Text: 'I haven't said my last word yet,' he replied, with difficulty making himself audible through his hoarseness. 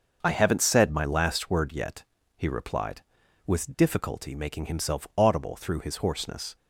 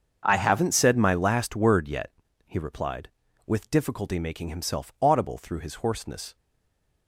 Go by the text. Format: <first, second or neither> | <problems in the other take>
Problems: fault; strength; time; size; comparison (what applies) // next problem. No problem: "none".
first | starts louder than the rest; until 1.2 s; 7 dB; also in the first // stays silent after the last word; slight; from 6.3 s on; 0.7 s long